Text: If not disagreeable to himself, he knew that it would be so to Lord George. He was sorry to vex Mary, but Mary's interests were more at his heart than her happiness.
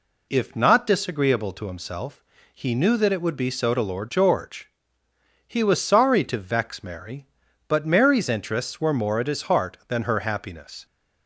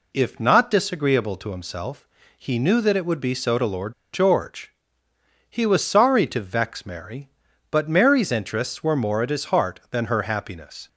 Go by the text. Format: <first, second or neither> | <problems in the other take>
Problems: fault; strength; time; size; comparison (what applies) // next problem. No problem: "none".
first | pauses between "Lord" and "George"; slight; at 3.9 s; 0.20 s long